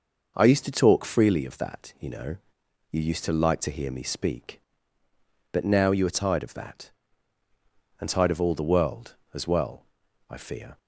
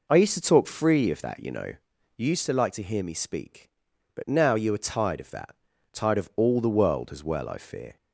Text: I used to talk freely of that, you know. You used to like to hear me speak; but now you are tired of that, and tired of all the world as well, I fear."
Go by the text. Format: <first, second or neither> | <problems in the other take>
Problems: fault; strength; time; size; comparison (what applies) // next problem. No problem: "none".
first | skips "and"; at 5.7 s